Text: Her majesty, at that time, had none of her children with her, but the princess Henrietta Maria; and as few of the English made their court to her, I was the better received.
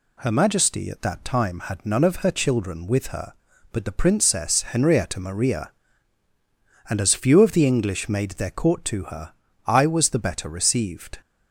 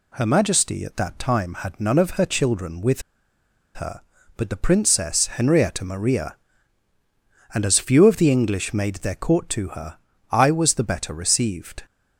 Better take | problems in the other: first | pauses between "with" and "her"; noticeable; at 3.0 s; 0.73 s long

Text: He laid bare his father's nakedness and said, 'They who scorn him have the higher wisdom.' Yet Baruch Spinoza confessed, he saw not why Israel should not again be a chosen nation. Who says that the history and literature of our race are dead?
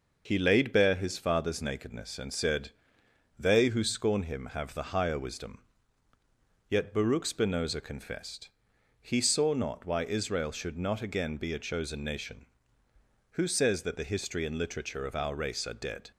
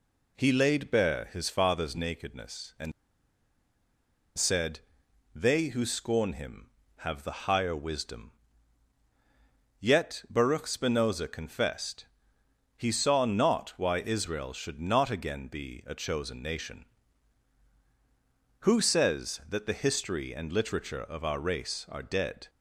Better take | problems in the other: first | pauses between "and" and "said"; strong; at 2.9 s; 1.4 s long

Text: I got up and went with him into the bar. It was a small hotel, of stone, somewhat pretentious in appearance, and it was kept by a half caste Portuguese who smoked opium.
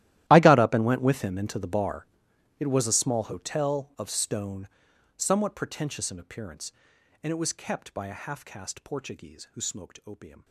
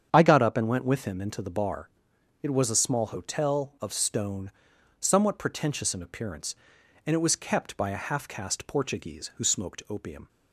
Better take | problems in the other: second | gets quieter; strong; throughout; 20.5 dB // starts louder than the rest; strong; until 1.2 s; 14 dB; strong in the second

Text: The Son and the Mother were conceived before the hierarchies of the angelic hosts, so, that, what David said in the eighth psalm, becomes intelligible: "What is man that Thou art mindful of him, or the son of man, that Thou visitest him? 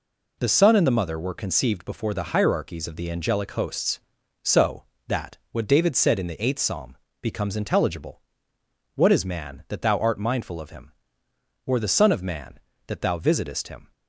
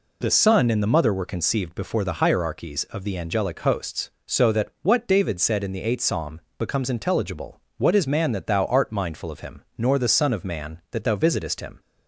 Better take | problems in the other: first | says "nor" for "or"; at 9.7 s

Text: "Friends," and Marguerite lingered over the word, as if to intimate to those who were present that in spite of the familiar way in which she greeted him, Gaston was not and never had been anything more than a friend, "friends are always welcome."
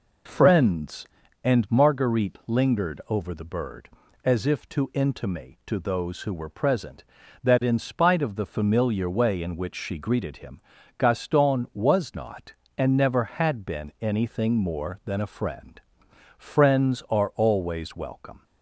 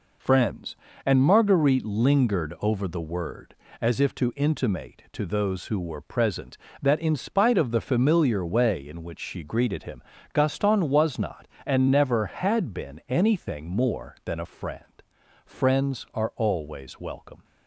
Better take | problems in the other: second | says "bird" for "word"; at 3.4 s

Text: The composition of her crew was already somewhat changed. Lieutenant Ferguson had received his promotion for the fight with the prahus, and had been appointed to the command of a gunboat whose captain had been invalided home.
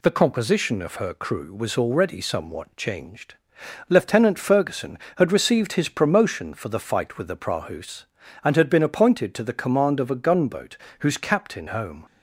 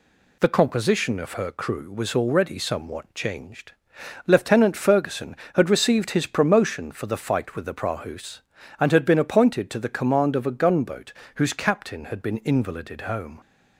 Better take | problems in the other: second | pauses between "gunboat" and "whose"; slight; at 10.7 s; 0.22 s long; slight in the second // skips "had been invalided"; at 11.6 s

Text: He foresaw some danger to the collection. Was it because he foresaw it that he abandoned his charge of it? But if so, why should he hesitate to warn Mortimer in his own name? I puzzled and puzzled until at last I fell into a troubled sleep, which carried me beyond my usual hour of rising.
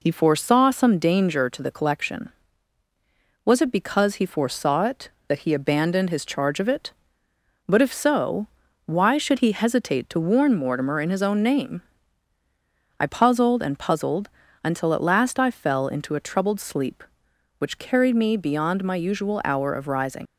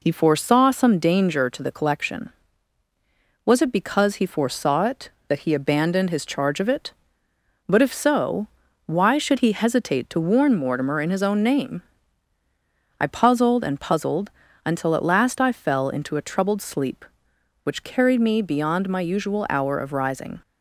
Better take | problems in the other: second | pauses between "puzzled" and "until"; slight; at 14.2 s; 0.36 s long; slight in the second // leaves "rising" unfinished; at 20.2 s; 110 ms

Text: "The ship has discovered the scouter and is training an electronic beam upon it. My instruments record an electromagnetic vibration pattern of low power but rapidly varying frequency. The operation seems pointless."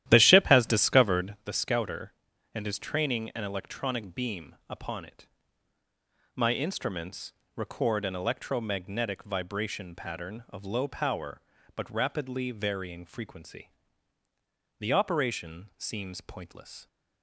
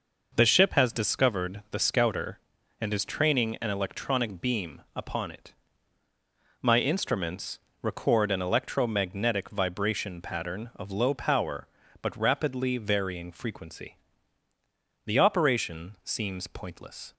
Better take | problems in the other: second | starts louder than the rest; strong; until 1.4 s; 12.5 dB // pauses between "instruments" and "record"; slight; at 7.3 s; 0.24 s long; slight in the second

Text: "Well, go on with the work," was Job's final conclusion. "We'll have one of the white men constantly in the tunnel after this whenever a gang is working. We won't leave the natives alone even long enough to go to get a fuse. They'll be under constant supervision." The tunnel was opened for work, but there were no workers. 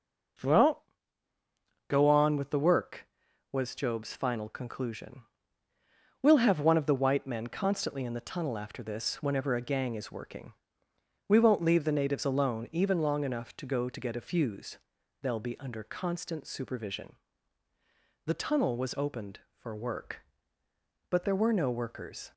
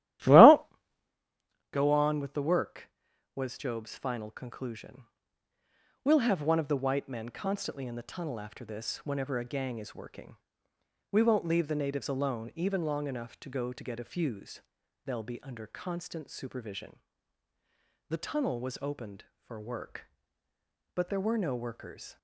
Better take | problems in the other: first | starts louder than the rest; strong; until 1.1 s; 13.5 dB

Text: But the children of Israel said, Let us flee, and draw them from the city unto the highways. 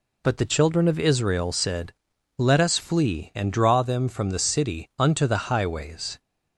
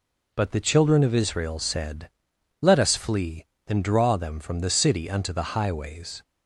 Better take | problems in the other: neither | none

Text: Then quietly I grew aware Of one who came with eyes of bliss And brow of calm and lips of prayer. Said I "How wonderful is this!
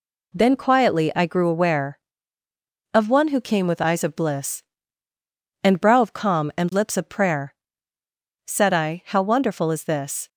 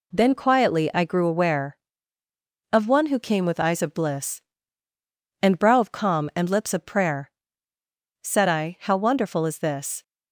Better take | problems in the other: neither | none

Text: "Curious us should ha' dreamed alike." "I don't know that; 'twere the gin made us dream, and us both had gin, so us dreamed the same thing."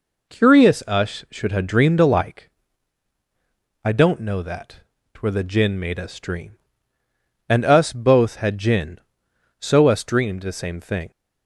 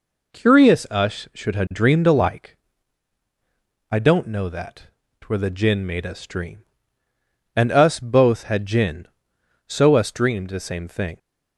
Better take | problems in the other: neither | none

